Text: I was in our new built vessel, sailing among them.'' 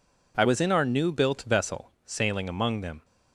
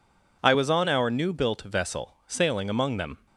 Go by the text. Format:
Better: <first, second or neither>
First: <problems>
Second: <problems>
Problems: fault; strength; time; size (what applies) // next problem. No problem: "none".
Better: first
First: none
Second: says "on" for "in"; at 0.6 s